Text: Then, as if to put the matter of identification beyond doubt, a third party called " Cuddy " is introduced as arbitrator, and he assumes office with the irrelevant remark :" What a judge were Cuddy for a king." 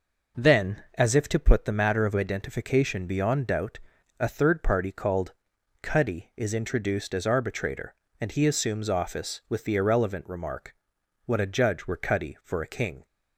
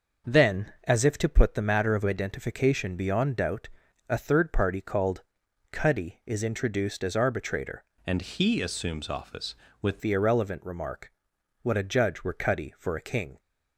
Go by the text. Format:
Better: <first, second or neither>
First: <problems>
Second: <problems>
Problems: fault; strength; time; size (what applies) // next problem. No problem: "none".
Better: first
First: none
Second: changes voice from "and" to "with"; from 8.0 to 9.9 s; 1.9 s long